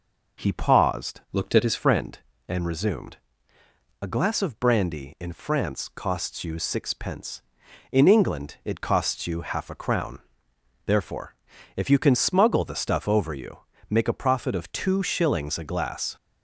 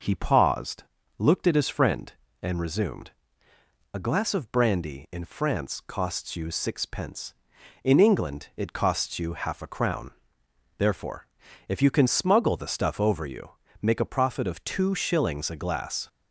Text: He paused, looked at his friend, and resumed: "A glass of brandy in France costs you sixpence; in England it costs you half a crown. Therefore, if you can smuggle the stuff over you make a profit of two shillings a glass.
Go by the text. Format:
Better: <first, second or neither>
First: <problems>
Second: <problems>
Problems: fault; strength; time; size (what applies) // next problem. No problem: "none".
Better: second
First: changes voice from "looked" to "his"; from 1.3 to 1.7 s; 0.4 s long // pauses between "you" and "make"; slight; at 13.6 s; 0.28 s long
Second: pauses between "you" and "make"; slight; at 13.5 s; 0.28 s long